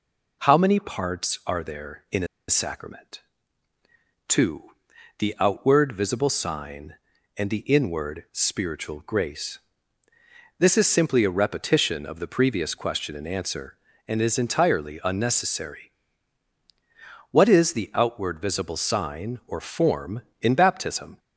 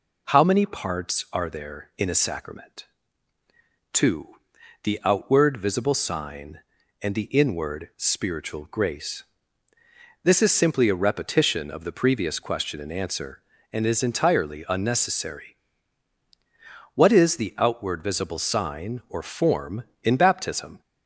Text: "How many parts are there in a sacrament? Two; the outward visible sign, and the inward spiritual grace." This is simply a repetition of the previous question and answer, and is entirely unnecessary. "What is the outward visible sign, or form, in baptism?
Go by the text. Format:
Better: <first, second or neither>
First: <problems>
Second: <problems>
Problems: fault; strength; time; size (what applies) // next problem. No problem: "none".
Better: second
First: pauses between "a" and "sacrament"; slight; at 2.2 s; 0.23 s long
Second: none